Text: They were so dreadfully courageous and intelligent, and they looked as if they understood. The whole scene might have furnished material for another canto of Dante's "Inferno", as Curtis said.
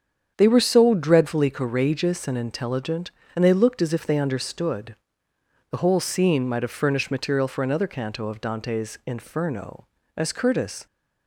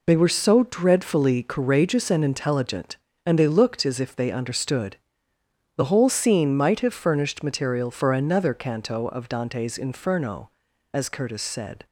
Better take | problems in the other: second | starts louder than the rest; strong; until 1.3 s; 7.5 dB // stops before "said"; at 10.8 s

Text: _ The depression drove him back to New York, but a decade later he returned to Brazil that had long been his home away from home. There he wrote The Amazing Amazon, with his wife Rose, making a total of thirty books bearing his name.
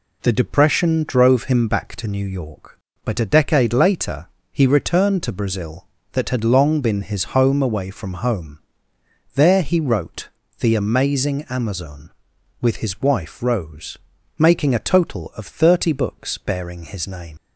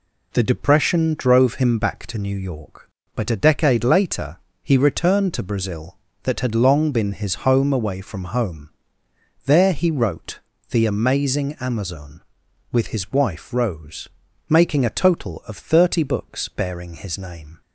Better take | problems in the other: second | pauses between "later" and "he"; slight; at 4.2 s; 0.24 s long; slight in the second // pauses between "wrote" and "The"; slight; at 10.2 s; 0.30 s long; slight in the second // leaves "name" unfinished; at 17.3 s; 130 ms

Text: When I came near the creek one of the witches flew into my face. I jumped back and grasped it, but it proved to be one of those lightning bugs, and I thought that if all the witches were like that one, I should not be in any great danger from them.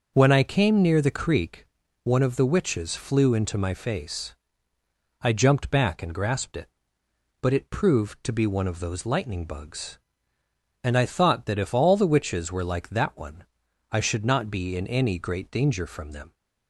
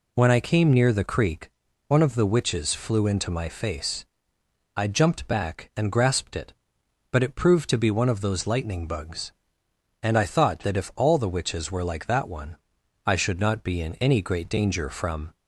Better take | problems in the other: first | pauses between "creek" and "one"; at 1.4 s; 0.38 s long; also in the first // stops before "them"; at 15.3 s

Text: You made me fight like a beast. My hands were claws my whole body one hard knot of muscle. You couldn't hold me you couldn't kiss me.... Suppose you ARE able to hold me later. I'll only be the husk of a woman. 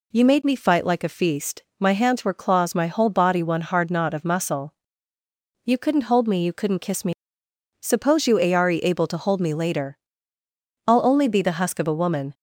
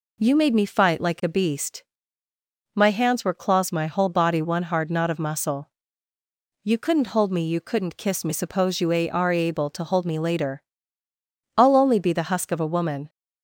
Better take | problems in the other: second | says "feast" for "beast"; at 1.1 s

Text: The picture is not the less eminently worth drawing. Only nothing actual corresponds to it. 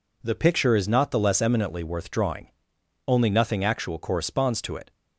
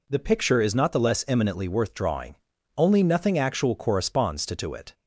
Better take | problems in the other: first | says "to" twice; at 4.5 s

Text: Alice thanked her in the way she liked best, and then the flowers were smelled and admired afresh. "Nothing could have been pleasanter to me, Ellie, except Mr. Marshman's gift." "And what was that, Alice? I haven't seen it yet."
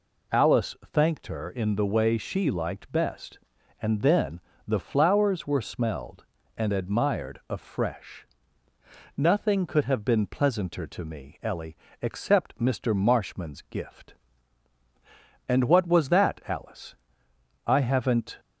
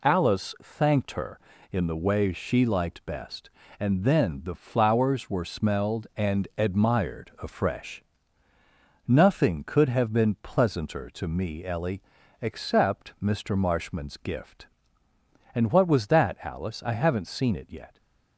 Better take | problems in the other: second | pauses between "Alice" and "thanked"; slight; at 0.7 s; 0.18 s long // pauses between "then" and "the"; slight; at 4.3 s; 0.28 s long // stops before "seen it yet"; at 18.3 s

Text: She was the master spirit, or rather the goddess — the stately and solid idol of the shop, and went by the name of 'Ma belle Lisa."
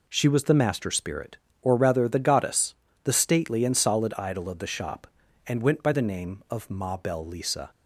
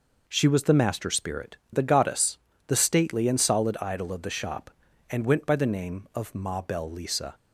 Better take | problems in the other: first | skips "or rather"; at 1.6 s

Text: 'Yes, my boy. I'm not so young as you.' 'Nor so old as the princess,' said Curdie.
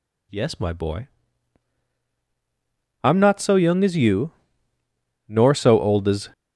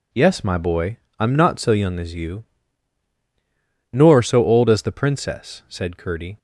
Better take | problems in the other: second | stops before "the princess said Curdie"; at 6.3 s

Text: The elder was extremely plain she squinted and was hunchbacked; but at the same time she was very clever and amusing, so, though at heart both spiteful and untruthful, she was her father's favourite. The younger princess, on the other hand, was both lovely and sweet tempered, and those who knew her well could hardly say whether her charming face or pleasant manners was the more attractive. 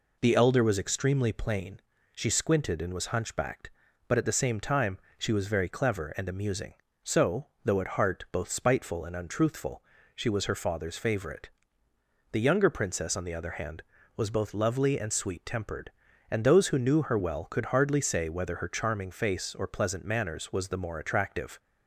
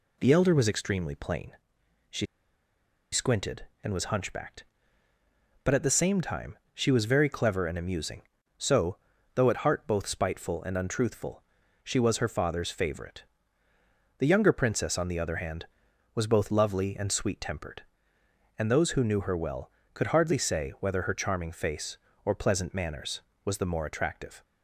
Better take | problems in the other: first | pauses between "plain" and "she"; noticeable; at 1.5 s; 0.58 s long; slight in the first // pauses between "she" and "squinted"; noticeable; at 2.2 s; 0.87 s long // pauses between "time" and "she"; slight; at 6.5 s; 0.16 s long; slight in the first

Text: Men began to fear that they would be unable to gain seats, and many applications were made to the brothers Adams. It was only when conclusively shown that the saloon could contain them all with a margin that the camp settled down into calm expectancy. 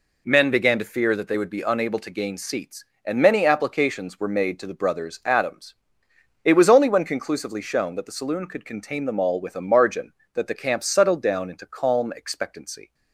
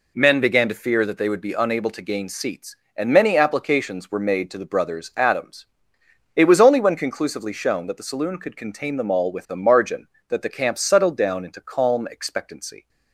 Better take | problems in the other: neither | none

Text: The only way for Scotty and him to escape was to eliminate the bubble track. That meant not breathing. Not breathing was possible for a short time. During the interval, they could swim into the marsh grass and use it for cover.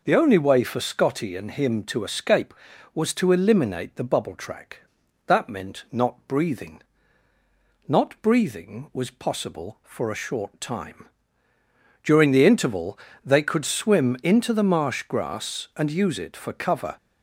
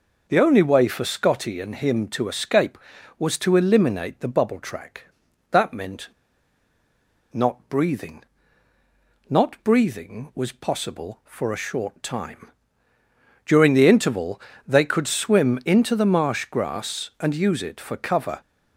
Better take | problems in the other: first | pauses between "meant" and "not"; at 6.0 s; 1.2 s long

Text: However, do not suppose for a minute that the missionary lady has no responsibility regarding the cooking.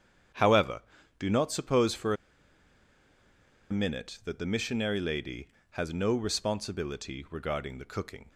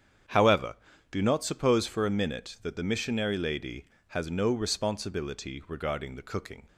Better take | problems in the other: second | starts louder than the rest; strong; until 1.7 s; 8.5 dB; strong in the second // pauses between "for" and "a"; strong; at 2.1 s; 1.5 s long

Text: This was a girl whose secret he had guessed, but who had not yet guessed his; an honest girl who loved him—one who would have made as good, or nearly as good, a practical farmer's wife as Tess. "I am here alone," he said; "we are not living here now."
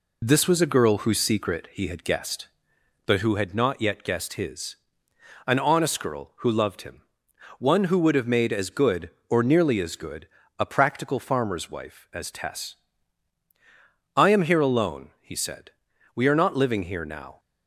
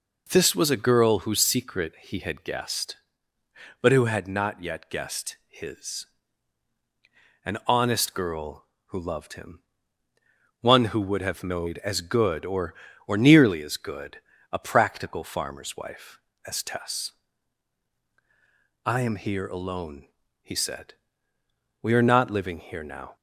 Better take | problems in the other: first | says "or" twice; at 13.0 s

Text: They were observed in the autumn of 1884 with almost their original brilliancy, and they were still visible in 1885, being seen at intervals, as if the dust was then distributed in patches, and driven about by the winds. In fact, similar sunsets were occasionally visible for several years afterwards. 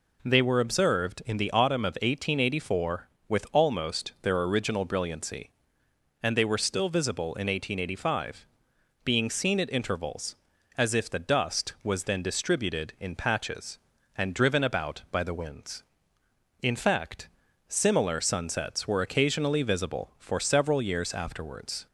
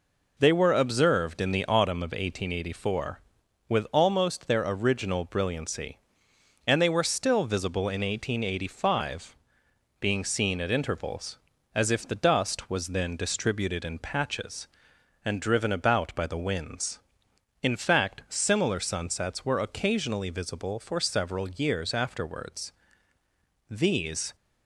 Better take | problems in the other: first | goes on to say "These"; noticeable; from 23.7 s on; 0.64 s long

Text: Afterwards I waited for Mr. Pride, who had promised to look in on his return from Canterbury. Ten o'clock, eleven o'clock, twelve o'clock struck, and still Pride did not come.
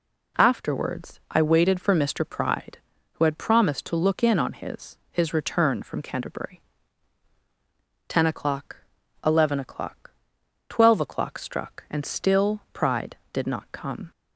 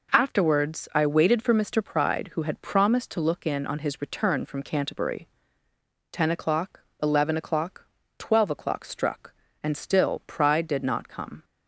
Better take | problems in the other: second | says "his" twice; at 5.1 s

